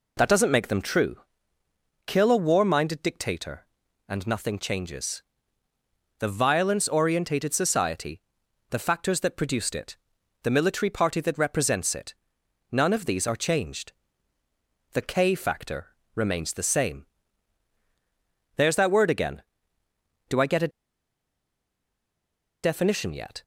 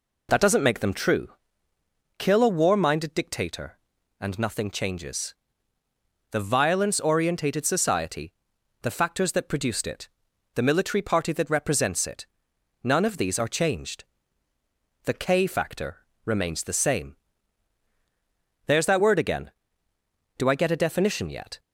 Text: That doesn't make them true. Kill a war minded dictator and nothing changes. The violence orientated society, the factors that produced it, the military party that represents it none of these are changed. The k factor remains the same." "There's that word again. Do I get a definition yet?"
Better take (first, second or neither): second